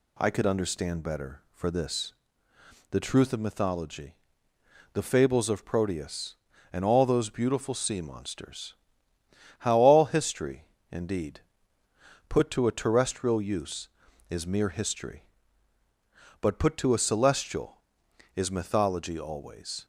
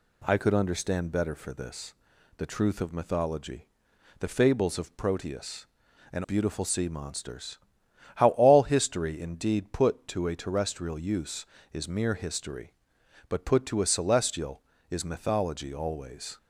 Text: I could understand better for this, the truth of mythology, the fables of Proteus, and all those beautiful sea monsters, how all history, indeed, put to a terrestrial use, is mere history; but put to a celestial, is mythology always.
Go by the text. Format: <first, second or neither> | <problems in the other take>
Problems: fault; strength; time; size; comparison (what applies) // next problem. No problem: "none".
first | skips "all those"; at 6.2 s